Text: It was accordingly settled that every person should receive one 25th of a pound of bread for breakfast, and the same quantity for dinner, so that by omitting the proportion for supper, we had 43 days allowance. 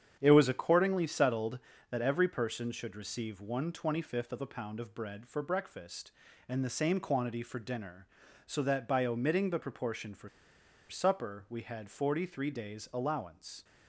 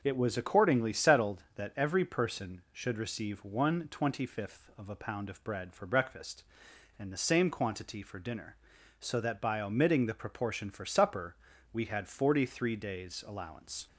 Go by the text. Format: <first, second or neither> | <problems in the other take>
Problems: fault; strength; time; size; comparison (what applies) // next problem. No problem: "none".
second | starts louder than the rest; strong; until 1.2 s; 8.5 dB // pauses between "for" and "supper"; noticeable; at 10.2 s; 0.61 s long